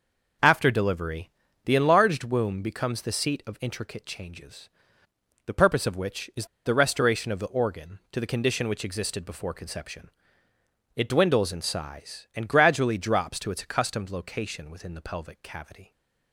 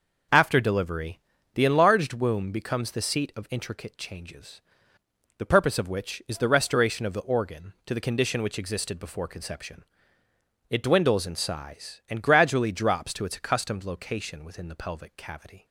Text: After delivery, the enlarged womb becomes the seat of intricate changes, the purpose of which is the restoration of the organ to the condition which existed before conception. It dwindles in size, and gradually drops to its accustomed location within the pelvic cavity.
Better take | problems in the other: second | pauses between "is" and "the"; slight; at 6.4 s; 0.20 s long

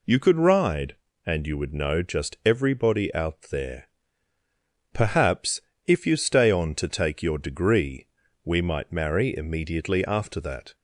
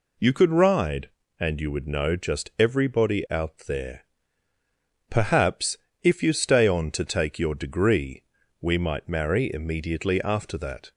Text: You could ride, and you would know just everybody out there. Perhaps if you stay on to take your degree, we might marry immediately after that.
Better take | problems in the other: neither | pauses between "Perhaps" and "if"; slight; the same in both

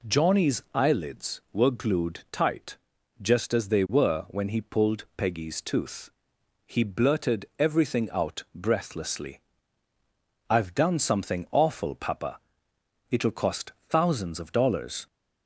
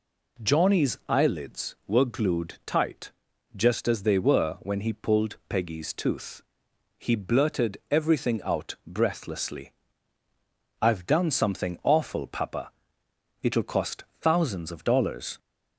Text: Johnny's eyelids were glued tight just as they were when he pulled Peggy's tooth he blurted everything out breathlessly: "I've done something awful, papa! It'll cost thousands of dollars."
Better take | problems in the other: neither | pauses between "tight" and "just"; the same in both // pauses between "tooth" and "he"; noticeable; the same in both

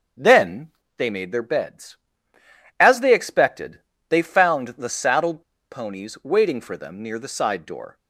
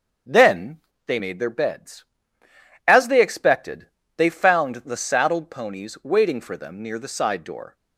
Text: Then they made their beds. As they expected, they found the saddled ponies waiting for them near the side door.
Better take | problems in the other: second | starts louder than the rest; until 1.4 s; 7 dB; also in the second // pauses between "Then" and "they"; slight; at 0.7 s; 0.26 s long; slight in the second // pauses between "saddled" and "ponies"; slight; at 5.4 s; 0.27 s long

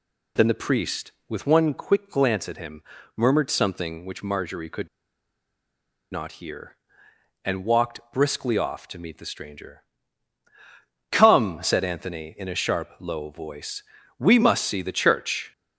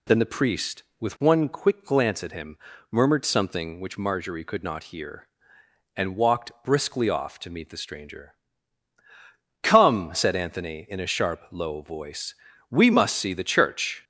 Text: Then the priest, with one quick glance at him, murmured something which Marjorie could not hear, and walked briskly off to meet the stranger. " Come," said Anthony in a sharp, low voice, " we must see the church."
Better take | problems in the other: second | pauses between "could" and "not"; strong; at 4.8 s; 1.2 s long

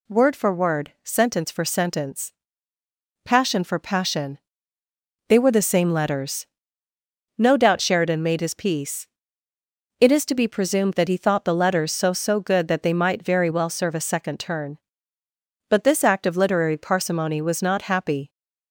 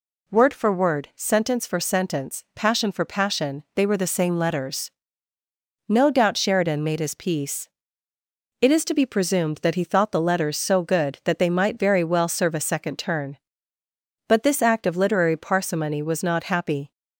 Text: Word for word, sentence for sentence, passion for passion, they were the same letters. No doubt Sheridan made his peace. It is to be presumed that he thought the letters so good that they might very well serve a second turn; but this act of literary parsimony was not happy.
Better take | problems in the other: second | says "so" twice; at 12.1 s

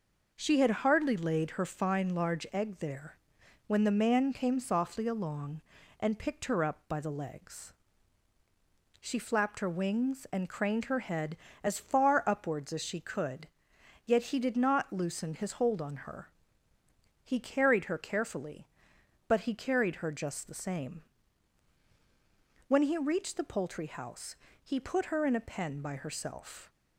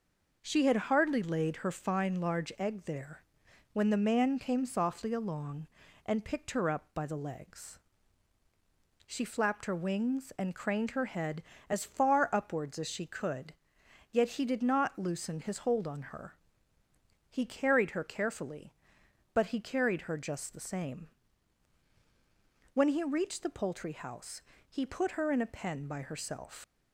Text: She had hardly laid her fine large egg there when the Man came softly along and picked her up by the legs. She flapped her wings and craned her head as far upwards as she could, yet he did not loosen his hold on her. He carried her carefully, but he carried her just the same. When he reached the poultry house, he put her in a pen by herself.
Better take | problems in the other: first | pauses between "there" and "when"; noticeable; at 3.2 s; 0.50 s long; noticeable in the first // leaves "herself" unfinished; at 26.6 s; 110 ms

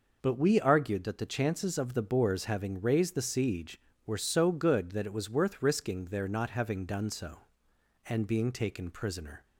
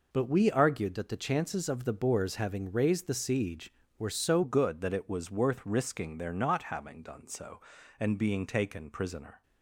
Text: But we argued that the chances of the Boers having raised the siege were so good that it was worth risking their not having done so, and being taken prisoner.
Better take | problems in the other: first | changes voice at "good"; from 4.4 s on; 5.0 s long

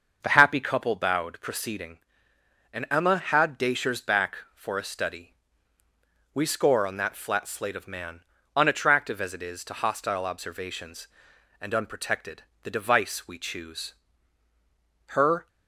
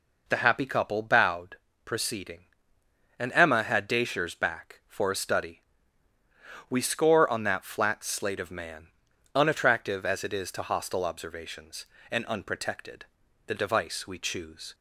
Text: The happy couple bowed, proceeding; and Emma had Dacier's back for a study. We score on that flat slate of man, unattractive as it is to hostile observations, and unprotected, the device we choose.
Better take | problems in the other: second | starts louder than the rest; until 1.2 s; 6 dB // goes on to say "Her"; slight; from 15.0 s on; 0.40 s long

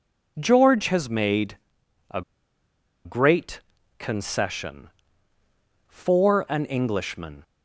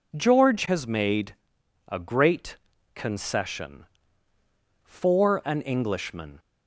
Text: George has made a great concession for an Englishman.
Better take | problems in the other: second | pauses between "made" and "a"; noticeable; at 1.5 s; 0.54 s long; noticeable in the second // pauses between "a" and "great"; noticeable; at 2.2 s; 0.83 s long // pauses between "great" and "concession"; at 3.6 s; 0.38 s long; also in the second

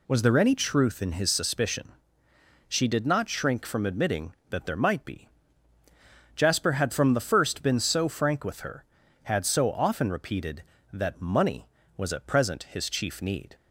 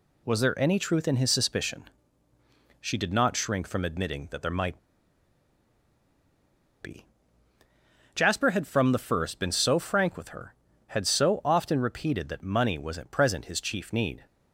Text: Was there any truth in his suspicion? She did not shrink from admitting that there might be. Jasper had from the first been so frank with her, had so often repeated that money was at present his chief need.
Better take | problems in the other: first | pauses between "might" and "be"; strong; at 4.7 s; 2.0 s long

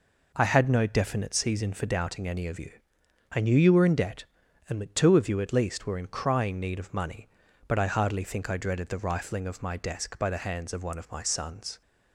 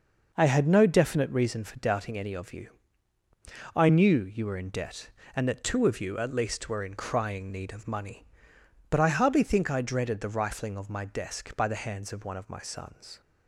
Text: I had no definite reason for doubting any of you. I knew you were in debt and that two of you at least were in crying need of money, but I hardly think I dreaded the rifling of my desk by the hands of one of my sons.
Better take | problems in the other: second | says "season" for "reason"; at 1.3 s

